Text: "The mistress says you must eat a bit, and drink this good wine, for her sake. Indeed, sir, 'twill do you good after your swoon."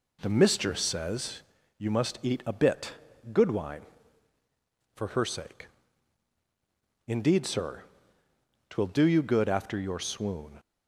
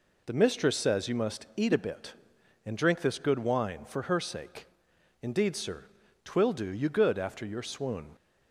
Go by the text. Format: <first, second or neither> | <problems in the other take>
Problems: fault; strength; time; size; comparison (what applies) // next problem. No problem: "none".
second | pauses between "says" and "you"; slight; at 1.4 s; 0.36 s long // skips "and drink this"; at 3.1 s